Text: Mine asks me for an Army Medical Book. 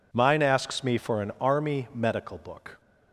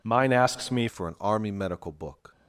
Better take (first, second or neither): first